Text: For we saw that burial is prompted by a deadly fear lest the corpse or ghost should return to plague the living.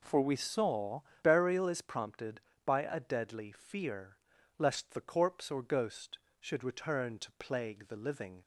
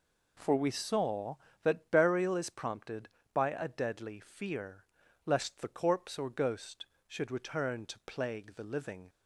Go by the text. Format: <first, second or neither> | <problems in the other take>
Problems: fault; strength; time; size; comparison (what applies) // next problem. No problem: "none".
second | skips "that"; at 1.1 s // pauses between "fear" and "lest"; at 4.1 s; 0.40 s long; also in the second